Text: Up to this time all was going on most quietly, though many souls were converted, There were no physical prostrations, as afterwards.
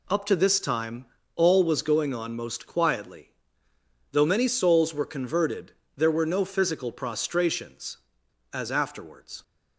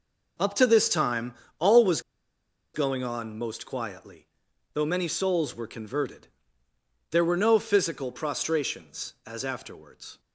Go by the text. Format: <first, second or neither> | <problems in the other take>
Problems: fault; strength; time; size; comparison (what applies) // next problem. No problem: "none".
first | pauses between "time" and "all"; slight; at 1.3 s; 0.24 s long; slight in the first // pauses between "was" and "going"; noticeable; at 1.9 s; 0.74 s long